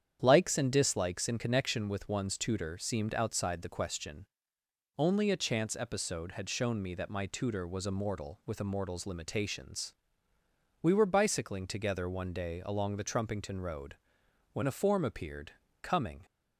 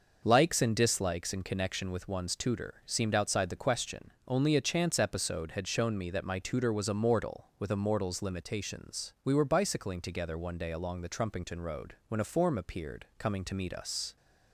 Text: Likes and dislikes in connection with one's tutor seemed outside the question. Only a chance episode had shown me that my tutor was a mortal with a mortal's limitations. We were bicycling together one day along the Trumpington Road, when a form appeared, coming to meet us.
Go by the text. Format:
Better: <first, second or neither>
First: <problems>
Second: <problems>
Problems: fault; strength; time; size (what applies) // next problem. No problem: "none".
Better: second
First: starts louder than the rest; strong; until 1.2 s; 9 dB // stops before "to meet us"; at 16.2 s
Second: none